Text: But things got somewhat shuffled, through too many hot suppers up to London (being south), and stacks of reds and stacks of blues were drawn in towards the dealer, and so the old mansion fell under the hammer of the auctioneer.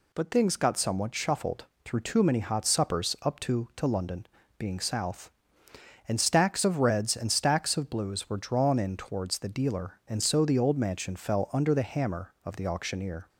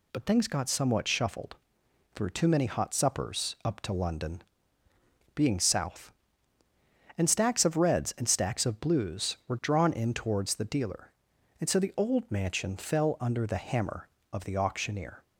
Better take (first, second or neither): second